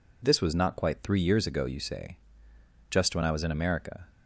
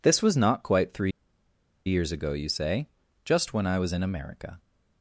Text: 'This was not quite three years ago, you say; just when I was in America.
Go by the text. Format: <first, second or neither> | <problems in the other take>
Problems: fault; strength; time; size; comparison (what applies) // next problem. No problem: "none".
first | pauses between "three" and "years"; noticeable; at 1.1 s; 0.76 s long